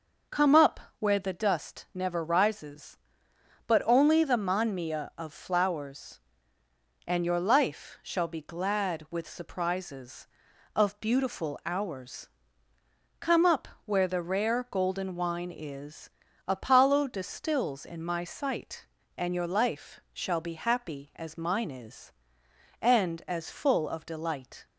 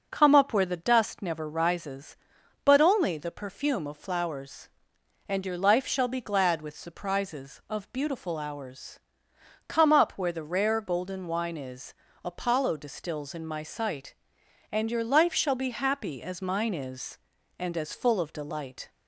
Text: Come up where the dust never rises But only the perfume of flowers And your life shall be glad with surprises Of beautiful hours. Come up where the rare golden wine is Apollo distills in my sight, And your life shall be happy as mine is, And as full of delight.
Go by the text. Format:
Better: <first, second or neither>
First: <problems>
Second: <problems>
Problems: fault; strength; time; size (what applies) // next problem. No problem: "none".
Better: second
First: starts louder than the rest; noticeable; until 1.5 s; 6 dB // pauses between "up" and "where"; slight; at 0.7 s; 0.20 s long // says "manmia" for "perfume"; at 4.3 s // pauses between "up" and "where"; slight; at 13.6 s; 0.18 s long // pauses between "is" and "Apollo"; slight; at 16.0 s; 0.36 s long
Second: starts louder than the rest; until 1.1 s; 6 dB // pauses between "is" and "Apollo"; slight; at 11.9 s; 0.32 s long